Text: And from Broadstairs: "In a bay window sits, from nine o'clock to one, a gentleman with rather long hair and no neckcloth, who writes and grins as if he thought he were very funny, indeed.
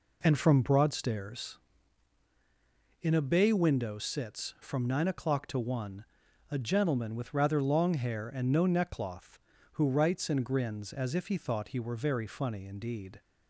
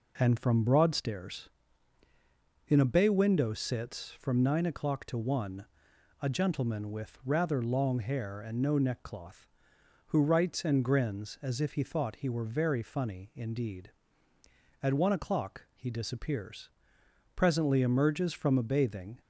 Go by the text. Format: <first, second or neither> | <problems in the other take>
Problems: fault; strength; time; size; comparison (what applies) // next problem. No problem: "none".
first | goes on to say "At one o'clock he disappears presently emerges from a bathing"; strong; from 14.8 s on; 4.3 s long